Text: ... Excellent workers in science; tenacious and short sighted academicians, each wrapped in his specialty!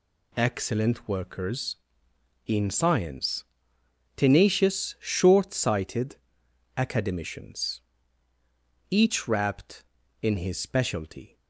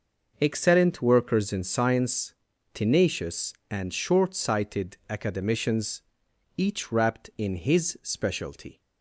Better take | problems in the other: second | skips "and"; at 4.9 s // pauses between "sighted" and "academicians"; noticeable; at 6.1 s; 0.60 s long

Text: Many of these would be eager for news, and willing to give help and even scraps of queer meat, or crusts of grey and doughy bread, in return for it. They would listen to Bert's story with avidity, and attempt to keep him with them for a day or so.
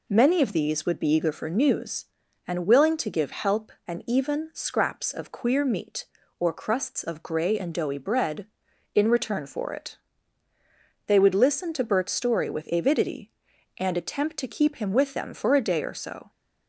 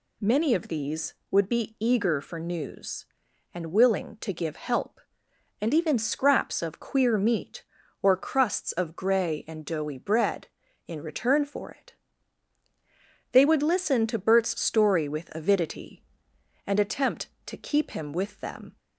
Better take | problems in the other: first | stops before "for a day or so"; at 18.7 s

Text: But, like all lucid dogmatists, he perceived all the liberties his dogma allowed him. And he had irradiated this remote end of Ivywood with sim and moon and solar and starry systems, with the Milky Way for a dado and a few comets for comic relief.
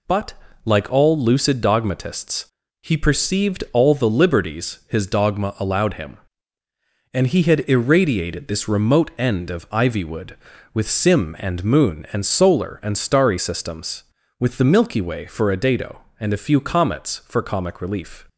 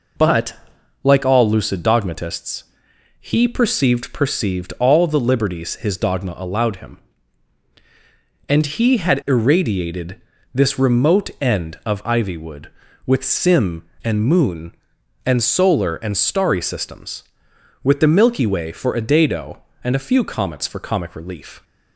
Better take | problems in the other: first | says "perceived" twice; at 4.1 s // pauses between "irradiated" and "this"; slight; at 10.1 s; 0.34 s long

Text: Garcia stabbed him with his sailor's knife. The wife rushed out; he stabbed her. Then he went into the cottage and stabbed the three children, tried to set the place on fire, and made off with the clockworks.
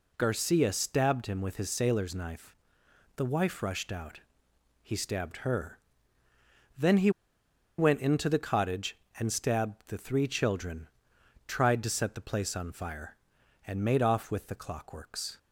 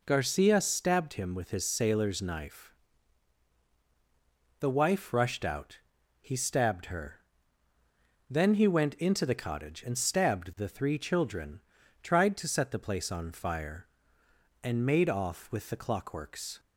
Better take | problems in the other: second | pauses between "he" and "went"; noticeable; at 7.0 s; 0.68 s long

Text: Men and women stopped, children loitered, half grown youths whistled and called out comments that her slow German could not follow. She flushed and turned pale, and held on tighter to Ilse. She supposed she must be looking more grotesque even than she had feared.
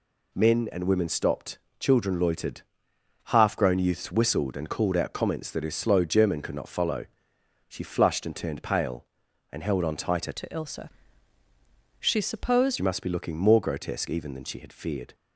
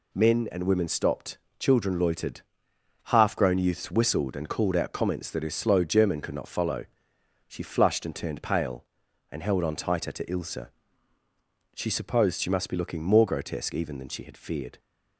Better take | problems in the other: second | changes voice from "to" to "supposed"; from 10.3 to 12.7 s; 2.4 s long

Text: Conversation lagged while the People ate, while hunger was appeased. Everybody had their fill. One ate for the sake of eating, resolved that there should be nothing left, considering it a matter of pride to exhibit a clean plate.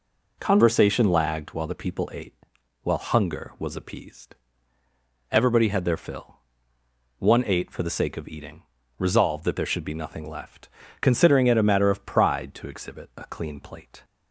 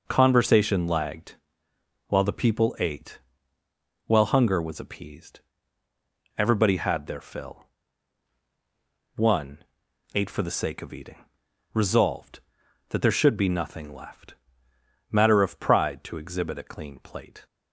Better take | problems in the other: first | pauses between "lagged" and "while"; noticeable; at 1.3 s; 0.72 s long // pauses between "One" and "ate"; noticeable; at 9.6 s; 0.50 s long // skips "considering it a"; at 14.7 s

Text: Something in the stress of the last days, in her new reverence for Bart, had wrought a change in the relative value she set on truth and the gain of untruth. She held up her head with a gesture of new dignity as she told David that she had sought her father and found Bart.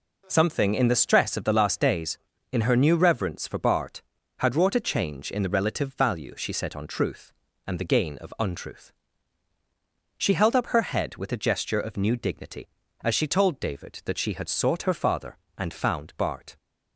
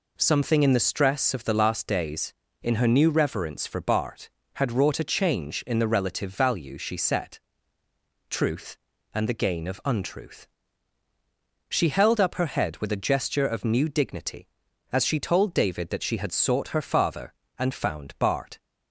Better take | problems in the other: first | skips "on"; at 7.8 s

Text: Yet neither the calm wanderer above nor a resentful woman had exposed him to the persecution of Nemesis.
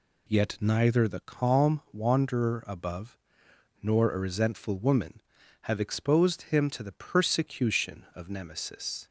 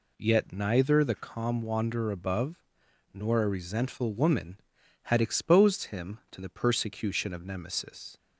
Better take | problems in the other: second | pauses between "above" and "nor"; noticeable; at 3.1 s; 0.64 s long; noticeable in the second // says "have" for "had"; at 5.6 s

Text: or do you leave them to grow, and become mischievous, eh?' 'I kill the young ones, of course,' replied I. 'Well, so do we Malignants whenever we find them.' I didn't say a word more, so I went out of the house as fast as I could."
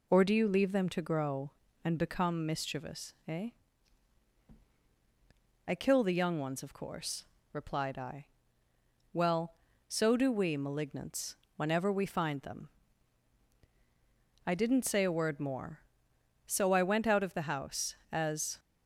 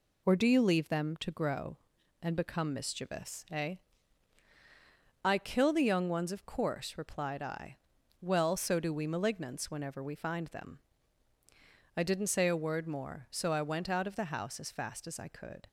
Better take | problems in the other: second | pauses between "Malignants" and "whenever"; slight; at 11.3 s; 0.22 s long // stops before "fast as I could"; at 18.5 s

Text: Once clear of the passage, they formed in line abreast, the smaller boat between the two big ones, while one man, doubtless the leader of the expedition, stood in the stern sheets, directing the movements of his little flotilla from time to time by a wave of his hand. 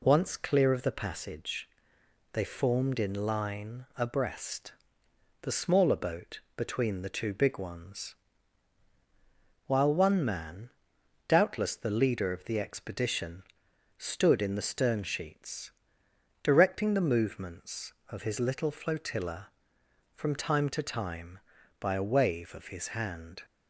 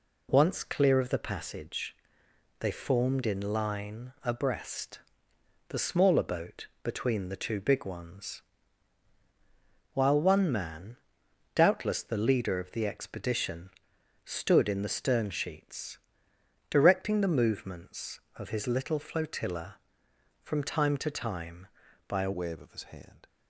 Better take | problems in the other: first | pauses between "boat" and "between"; slight; at 6.6 s; 0.16 s long; slight in the first // changes voice at "wave"; from 22.3 s on; 0.9 s long

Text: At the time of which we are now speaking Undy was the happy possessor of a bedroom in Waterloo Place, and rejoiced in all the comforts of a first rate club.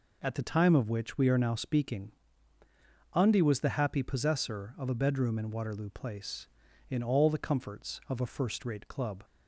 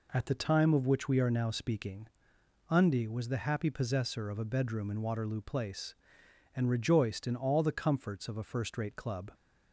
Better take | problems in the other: second | pauses between "speaking" and "Undy"; at 2.1 s; 1.0 s long; noticeable in the second // skips "and rejoiced"; at 6.6 s

